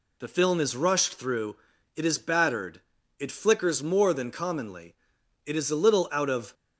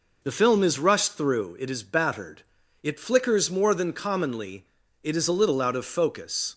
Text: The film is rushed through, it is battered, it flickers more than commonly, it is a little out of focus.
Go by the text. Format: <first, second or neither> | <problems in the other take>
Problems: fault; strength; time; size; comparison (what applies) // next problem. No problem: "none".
second | stops before "focus"; at 6.5 s